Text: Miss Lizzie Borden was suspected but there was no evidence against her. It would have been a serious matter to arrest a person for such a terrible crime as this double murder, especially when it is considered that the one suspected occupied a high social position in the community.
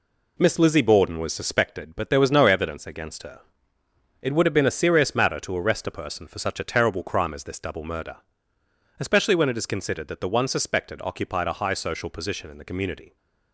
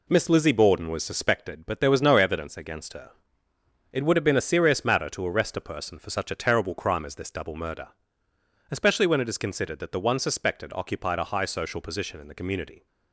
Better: neither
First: none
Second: none

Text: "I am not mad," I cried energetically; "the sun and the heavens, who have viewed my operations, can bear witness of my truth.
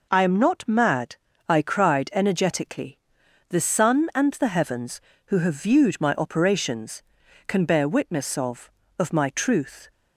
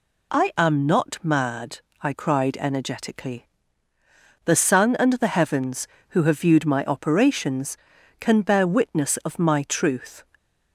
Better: second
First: says "of" twice; at 9.0 s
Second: none

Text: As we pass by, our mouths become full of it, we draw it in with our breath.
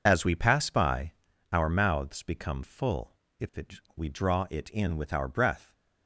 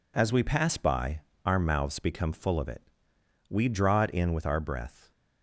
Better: second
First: says "if" for "of"; at 3.4 s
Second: none

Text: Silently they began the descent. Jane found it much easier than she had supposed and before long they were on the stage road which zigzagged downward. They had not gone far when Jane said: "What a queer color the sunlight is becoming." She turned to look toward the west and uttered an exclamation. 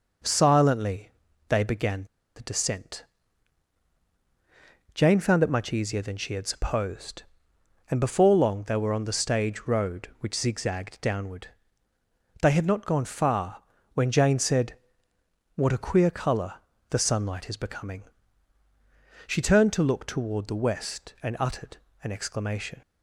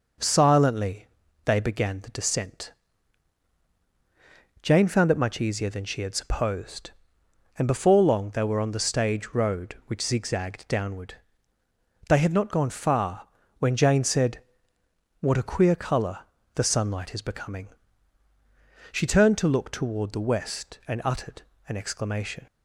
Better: second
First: pauses between "Silently" and "they"; at 1.1 s; 0.38 s long // pauses between "began" and "the"; slight; at 2.0 s; 0.31 s long // pauses between "far" and "when"; slight; at 13.6 s; 0.30 s long // pauses between "color" and "the"; slight; at 16.5 s; 0.34 s long // pauses between "uttered" and "an"; slight; at 21.7 s; 0.26 s long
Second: pauses between "Silently" and "they"; at 1.0 s; 0.38 s long // pauses between "far" and "when"; slight; at 13.2 s; 0.30 s long // pauses between "color" and "the"; slight; at 16.2 s; 0.34 s long // pauses between "uttered" and "an"; slight; at 21.4 s; 0.26 s long

